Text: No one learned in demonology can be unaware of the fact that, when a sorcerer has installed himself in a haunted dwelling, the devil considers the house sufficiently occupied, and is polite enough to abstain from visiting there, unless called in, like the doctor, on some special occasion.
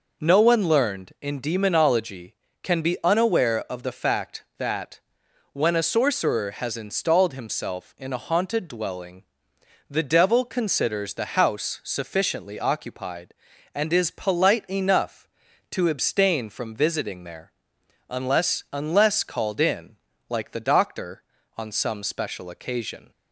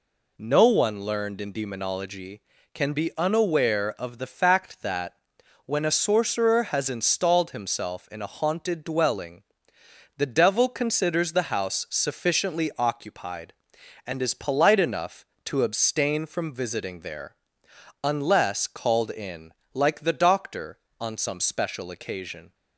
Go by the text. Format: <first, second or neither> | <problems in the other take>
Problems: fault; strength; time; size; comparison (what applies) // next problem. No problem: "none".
second | says "unless" twice; at 18.7 s